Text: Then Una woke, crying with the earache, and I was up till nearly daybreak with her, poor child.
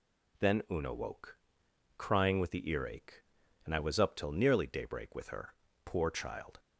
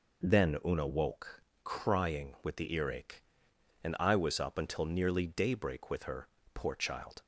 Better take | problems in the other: first | says "until" for "till"; at 4.5 s

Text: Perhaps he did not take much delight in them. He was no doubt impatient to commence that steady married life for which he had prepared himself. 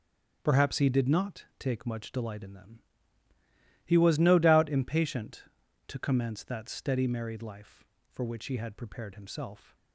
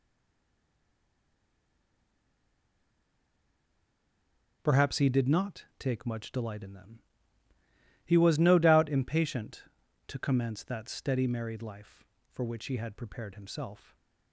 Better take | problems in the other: first | stays silent before the first word; strong; until 4.6 s; 4.6 s long // starts louder than the rest; strong; until 5.6 s; 8 dB; strong in the first

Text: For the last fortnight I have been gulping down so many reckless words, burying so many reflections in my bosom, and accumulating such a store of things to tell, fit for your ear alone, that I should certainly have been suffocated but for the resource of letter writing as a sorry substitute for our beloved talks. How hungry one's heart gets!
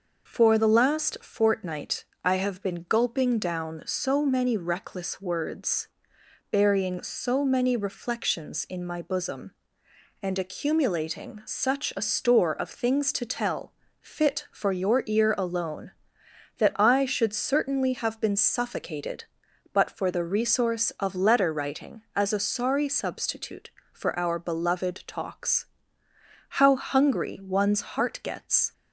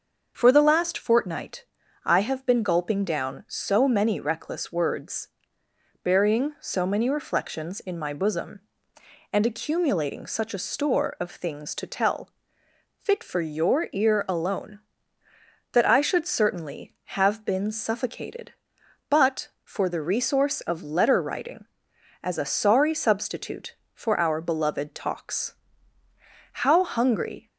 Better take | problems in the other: first | starts louder than the rest; until 1.3 s; 6.5 dB // pauses between "fortnight" and "I"; at 1.6 s; 0.40 s long; slight in the first // stops before "one's heart gets"; at 27.4 s

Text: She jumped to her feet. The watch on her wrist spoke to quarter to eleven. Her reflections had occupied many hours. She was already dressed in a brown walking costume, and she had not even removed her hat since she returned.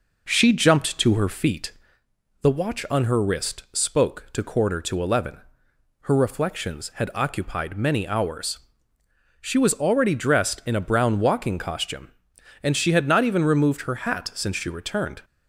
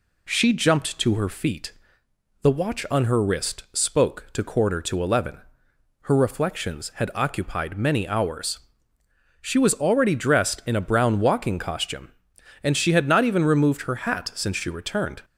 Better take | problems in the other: second | starts louder than the rest; noticeable; until 1.9 s; 5 dB

